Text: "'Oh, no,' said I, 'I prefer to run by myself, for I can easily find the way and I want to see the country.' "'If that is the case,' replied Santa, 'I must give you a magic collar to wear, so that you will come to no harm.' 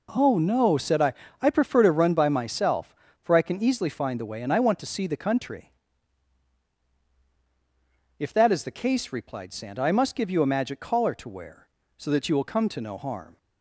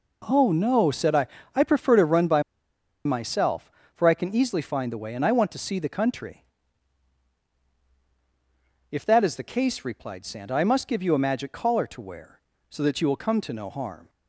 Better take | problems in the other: first | pauses between "by" and "myself"; noticeable; at 2.4 s; 0.64 s long

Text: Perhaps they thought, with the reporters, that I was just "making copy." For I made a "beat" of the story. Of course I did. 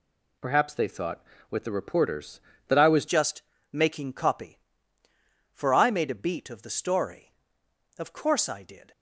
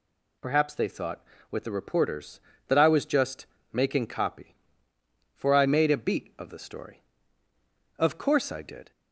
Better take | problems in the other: second | changes voice at "just"; from 3.0 s on; 5.9 s long // pauses between "just" and "making"; slight; at 3.4 s; 0.30 s long; slight in the second

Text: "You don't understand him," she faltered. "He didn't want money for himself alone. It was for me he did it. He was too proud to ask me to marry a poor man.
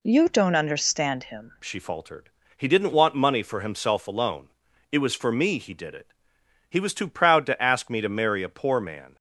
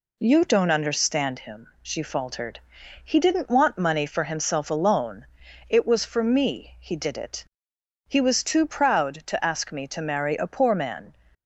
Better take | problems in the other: second | changes voice at "she"; from 1.6 s on; 7.5 s long

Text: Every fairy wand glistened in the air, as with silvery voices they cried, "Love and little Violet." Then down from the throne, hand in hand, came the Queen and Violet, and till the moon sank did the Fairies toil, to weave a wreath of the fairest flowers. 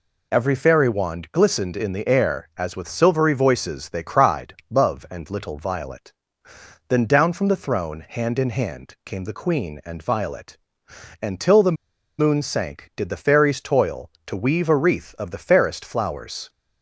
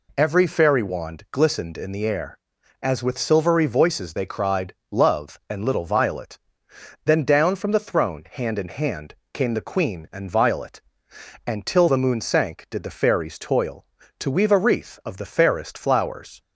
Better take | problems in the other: second | pauses between "the" and "moon"; at 11.7 s; 0.42 s long

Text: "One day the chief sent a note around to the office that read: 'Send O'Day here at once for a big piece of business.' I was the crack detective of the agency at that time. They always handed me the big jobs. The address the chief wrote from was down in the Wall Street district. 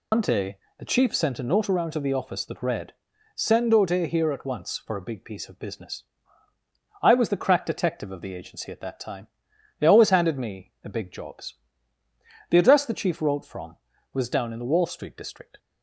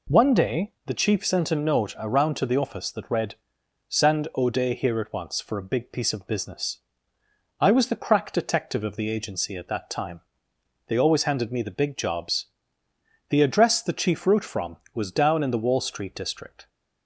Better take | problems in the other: second | loses the start of "One"; at 0.1 s; 100 ms // pauses between "day" and "the"; slight; at 0.5 s; 0.20 s long

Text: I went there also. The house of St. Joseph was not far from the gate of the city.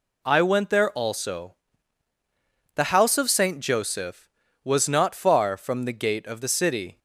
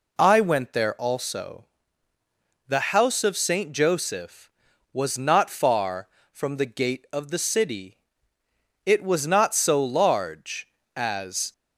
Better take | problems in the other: first | goes on to say "It was not so large as"; strong; from 8.8 s on; 2.6 s long

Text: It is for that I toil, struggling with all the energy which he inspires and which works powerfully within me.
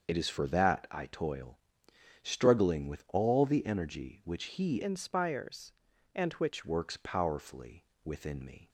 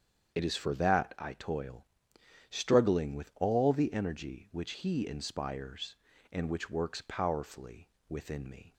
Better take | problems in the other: second | starts louder than the rest; until 1.1 s; 6.5 dB; strong in the second // changes voice from "inspires" to "which"; from 4.8 to 6.6 s; 1.8 s long // pauses between "powerfully" and "within"; slight; at 7.8 s; 0.22 s long; slight in the second

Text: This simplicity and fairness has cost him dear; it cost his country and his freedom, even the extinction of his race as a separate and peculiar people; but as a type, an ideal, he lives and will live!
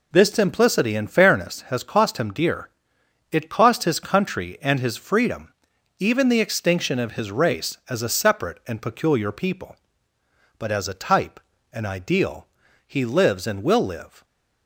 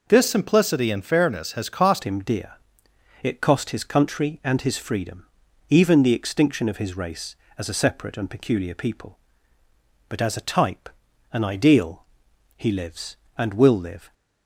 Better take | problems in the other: first | changes voice at "him"; from 2.0 s on; 12.1 s long

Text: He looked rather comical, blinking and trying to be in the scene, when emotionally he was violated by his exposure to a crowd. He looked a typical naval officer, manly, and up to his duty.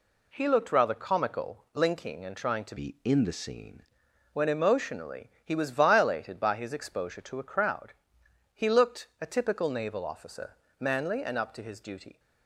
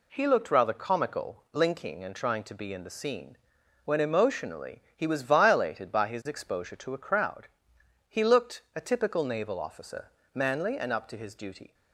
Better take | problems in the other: second | changes voice from "be" to "scene"; from 2.7 to 3.8 s; 1.1 s long // pauses between "emotionally" and "he"; slight; at 5.2 s; 0.16 s long; slight in the second

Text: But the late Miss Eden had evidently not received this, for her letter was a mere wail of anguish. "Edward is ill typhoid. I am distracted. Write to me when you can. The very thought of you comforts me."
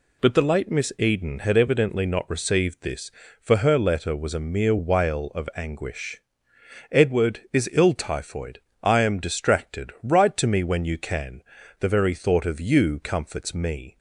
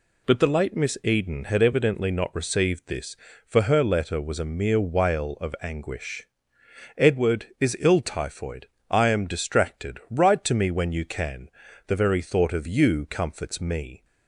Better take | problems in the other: neither | none

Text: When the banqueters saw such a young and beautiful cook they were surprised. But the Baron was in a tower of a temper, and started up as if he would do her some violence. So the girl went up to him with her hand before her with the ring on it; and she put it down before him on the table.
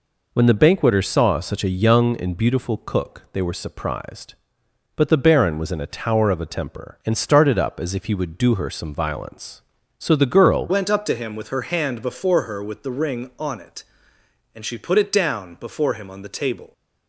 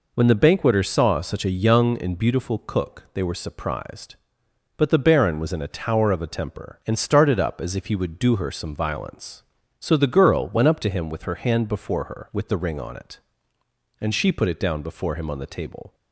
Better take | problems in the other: second | changes voice at "went"; from 10.6 s on; 6.1 s long

